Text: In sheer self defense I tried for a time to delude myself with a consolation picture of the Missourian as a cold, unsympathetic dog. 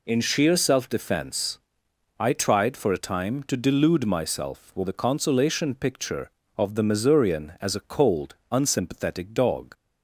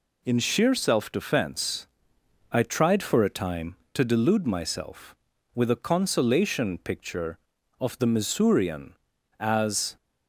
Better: first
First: pauses between "defense" and "I"; noticeable; at 1.5 s; 0.60 s long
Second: pauses between "defense" and "I"; noticeable; at 1.8 s; 0.66 s long // stops before "a cold unsympathetic dog"; at 9.9 s

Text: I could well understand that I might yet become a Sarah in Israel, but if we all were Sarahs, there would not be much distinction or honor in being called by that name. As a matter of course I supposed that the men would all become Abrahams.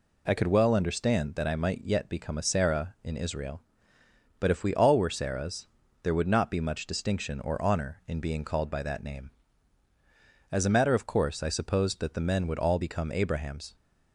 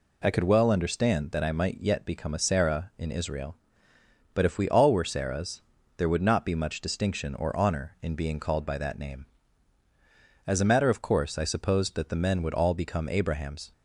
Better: neither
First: none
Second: none

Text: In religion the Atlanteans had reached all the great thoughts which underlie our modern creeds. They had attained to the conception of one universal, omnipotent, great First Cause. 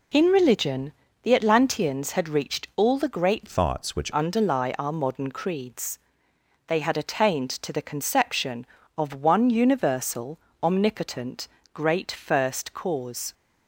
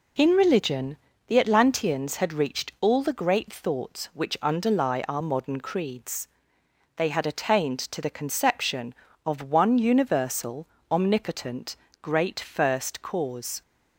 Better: second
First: pauses between "religion" and "the"; slight; at 0.9 s; 0.30 s long // changes voice from "thoughts" to "which"; from 3.4 to 4.1 s; 0.7 s long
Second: pauses between "religion" and "the"; slight; at 0.9 s; 0.30 s long

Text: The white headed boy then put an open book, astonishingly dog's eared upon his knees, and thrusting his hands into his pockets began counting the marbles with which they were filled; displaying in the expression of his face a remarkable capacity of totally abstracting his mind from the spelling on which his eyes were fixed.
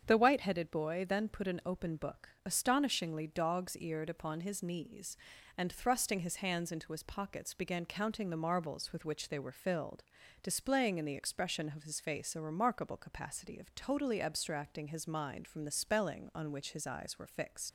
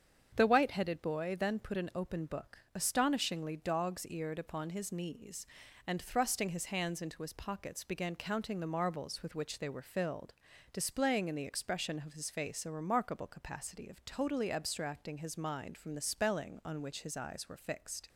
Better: second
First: starts louder than the rest; strong; until 1.1 s; 7.5 dB // leaves "fixed" unfinished; at 17.6 s; 80 ms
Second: starts louder than the rest; strong; until 1.3 s; 7.5 dB

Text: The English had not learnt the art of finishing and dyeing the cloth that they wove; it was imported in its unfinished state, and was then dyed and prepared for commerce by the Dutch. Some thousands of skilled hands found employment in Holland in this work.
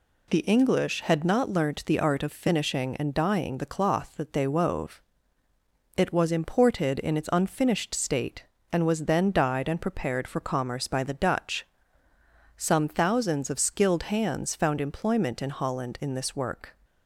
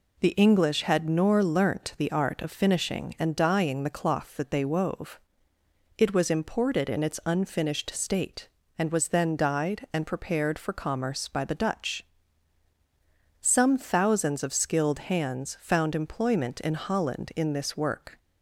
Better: first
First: none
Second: says "nor" for "not"; at 1.0 s

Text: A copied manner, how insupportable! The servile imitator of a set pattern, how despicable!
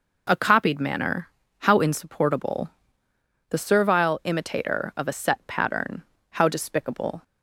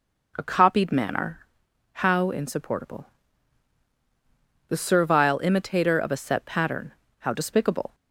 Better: neither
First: none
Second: none

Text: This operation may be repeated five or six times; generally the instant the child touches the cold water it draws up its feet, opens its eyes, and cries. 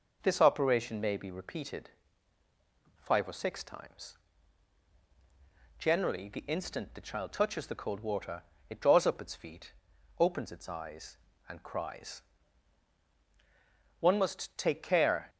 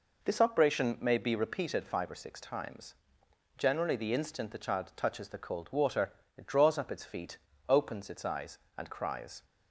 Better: second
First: pauses between "repeated" and "five"; at 1.8 s; 1.1 s long // pauses between "water" and "it"; slight; at 8.4 s; 0.26 s long // goes on to say "One must take care"; noticeable; from 13.9 s on; 1.3 s long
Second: pauses between "water" and "it"; slight; at 6.1 s; 0.24 s long

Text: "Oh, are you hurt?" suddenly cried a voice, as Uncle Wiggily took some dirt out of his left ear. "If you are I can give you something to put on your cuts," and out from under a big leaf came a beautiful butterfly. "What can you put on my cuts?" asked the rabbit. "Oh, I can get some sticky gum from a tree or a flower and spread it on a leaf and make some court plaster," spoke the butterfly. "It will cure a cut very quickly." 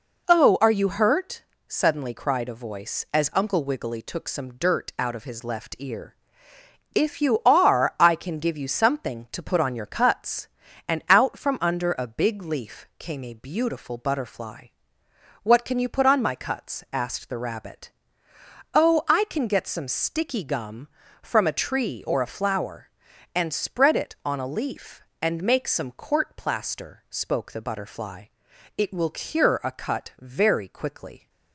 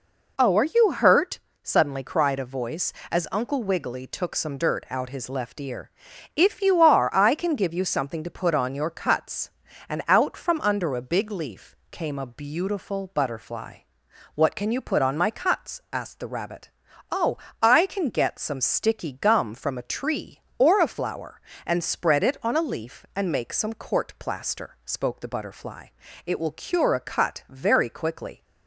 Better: first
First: none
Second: skips "of"; at 5.0 s

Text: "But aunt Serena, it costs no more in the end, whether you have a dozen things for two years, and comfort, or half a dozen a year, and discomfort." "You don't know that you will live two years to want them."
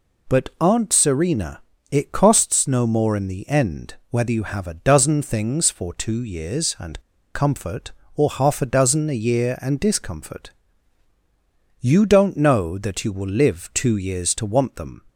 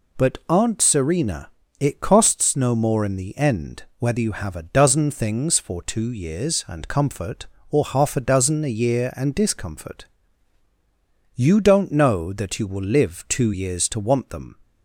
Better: second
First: pauses between "and" and "comfort"; slight; at 7.0 s; 0.33 s long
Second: none

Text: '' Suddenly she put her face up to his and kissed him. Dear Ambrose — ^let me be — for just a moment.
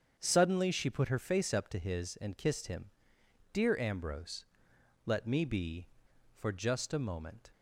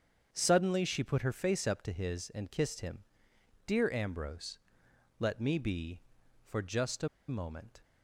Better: first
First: starts louder than the rest; until 1.1 s; 7 dB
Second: starts louder than the rest; until 1.3 s; 7 dB // pauses between "a" and "moment"; slight; at 7.0 s; 0.22 s long

